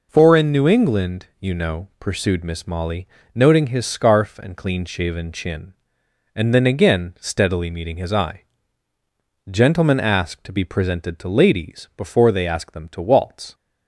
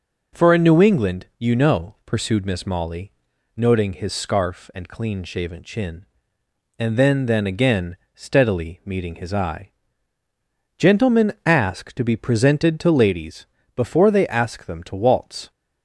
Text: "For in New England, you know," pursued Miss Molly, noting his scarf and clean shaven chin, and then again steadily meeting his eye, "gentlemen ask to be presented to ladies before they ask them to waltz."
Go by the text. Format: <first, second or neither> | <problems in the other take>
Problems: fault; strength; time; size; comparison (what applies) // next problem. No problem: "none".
first | says "then" twice; at 7.2 s // pauses between "again" and "steadily"; slight; at 7.9 s; 0.20 s long // pauses between "ladies" and "before"; slight; at 13.4 s; 0.30 s long